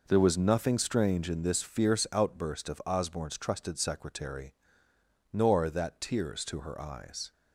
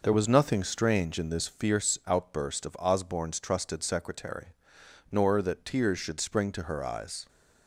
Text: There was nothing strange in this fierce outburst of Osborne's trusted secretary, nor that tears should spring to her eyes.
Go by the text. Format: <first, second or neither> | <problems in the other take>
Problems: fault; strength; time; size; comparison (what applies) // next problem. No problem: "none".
second | skips "should spring"; at 6.4 s